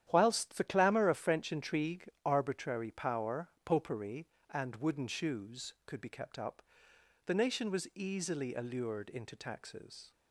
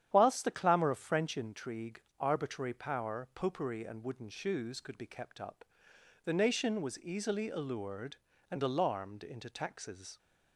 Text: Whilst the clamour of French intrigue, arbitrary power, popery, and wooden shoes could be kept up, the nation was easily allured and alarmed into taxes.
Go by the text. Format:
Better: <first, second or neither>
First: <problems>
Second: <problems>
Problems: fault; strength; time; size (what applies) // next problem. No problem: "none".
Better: second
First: starts louder than the rest; strong; until 1.1 s; 10.5 dB // skips "and alarmed"; at 9.0 s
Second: starts louder than the rest; strong; until 1.1 s; 10 dB